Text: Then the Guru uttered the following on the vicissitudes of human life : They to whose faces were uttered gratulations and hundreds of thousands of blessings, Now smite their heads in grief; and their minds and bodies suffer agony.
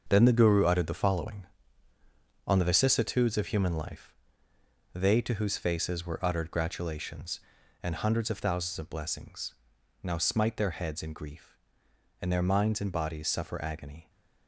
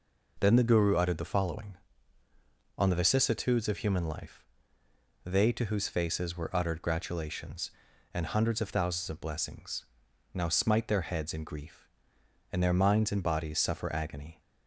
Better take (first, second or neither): second